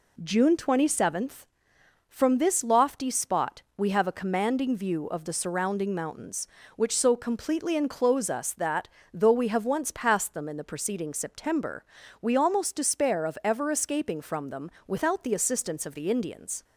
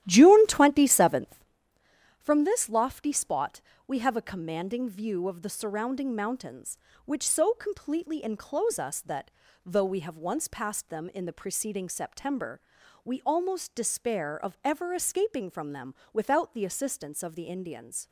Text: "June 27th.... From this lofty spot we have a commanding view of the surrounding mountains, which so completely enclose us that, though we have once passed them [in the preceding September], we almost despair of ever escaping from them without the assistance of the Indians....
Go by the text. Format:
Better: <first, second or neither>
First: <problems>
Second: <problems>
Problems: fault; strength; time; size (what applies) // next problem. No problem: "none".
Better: first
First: pauses between "spot" and "we"; slight; at 3.6 s; 0.16 s long // pauses between "them" and "without"; slight; at 14.7 s; 0.16 s long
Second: starts louder than the rest; strong; until 1.5 s; 13 dB // pauses between "spot" and "we"; slight; at 3.6 s; 0.26 s long // pauses between "them" and "without"; slight; at 15.9 s; 0.20 s long